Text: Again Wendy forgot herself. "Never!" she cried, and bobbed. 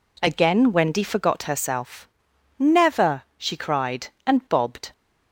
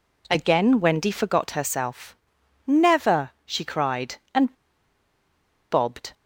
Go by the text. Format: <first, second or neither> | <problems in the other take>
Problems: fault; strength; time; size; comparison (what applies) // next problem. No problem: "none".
first | pauses between "and" and "bobbed"; at 4.5 s; 1.1 s long